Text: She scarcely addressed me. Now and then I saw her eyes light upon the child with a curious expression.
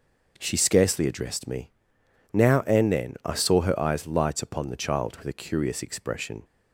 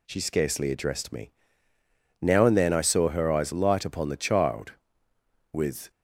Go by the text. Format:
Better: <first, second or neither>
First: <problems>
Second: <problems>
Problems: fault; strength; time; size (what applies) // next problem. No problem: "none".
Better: first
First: none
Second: stops before "a curious expression"; at 5.9 s